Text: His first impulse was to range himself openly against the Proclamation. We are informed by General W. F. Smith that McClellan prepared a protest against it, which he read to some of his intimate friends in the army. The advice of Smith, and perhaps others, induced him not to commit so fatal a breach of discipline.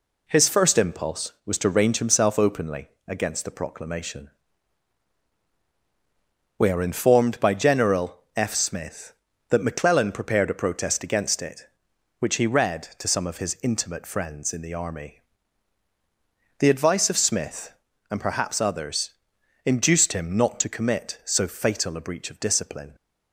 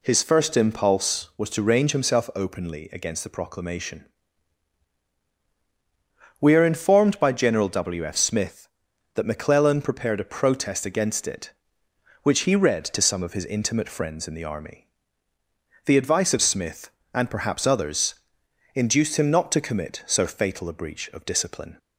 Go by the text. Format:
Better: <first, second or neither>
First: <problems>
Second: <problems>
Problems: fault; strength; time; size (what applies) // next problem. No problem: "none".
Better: second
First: pauses between "openly" and "against"; slight; at 2.8 s; 0.18 s long // skips "W"; at 8.2 s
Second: none